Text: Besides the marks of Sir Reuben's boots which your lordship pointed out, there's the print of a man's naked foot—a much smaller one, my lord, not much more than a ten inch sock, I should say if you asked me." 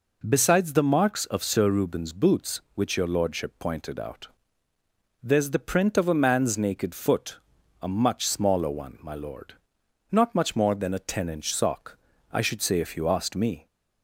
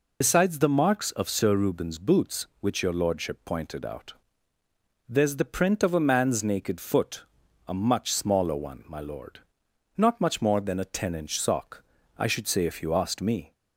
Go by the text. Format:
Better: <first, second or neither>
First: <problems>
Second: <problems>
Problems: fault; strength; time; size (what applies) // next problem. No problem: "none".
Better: first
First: none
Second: loses the start of "Besides"; at 0.2 s; 115 ms